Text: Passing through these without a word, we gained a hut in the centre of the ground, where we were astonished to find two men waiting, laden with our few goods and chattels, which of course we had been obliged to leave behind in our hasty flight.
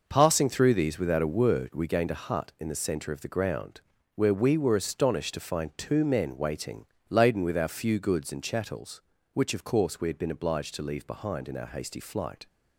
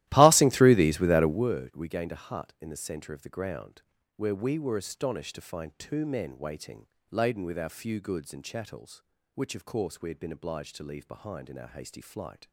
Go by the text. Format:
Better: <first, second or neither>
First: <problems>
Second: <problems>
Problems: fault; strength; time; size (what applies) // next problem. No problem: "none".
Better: first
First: none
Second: starts louder than the rest; strong; until 1.5 s; 15.5 dB